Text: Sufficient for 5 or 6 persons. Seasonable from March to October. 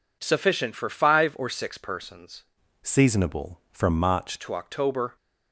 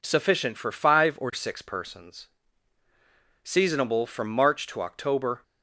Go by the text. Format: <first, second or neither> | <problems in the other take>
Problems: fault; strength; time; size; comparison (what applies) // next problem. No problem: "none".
second | changes voice from "Seasonable" to "March"; from 2.8 to 4.3 s; 1.5 s long